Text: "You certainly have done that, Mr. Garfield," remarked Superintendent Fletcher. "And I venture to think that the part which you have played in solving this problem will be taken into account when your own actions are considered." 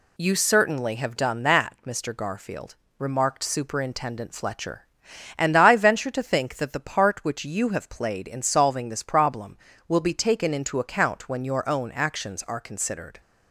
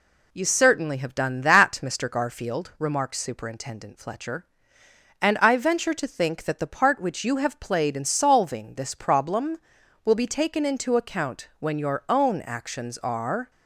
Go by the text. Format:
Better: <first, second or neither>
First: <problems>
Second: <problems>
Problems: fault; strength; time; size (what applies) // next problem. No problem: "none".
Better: first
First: none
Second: stops before "considered"; at 13.5 s